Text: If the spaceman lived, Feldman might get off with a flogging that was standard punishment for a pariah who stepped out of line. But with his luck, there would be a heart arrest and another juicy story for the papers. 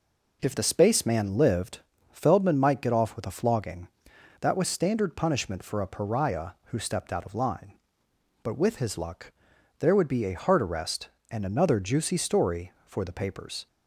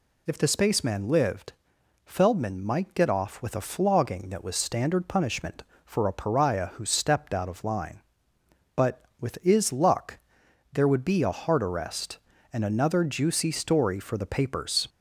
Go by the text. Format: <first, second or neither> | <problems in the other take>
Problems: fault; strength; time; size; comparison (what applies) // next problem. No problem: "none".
first | says "is" for "his"; at 9.4 s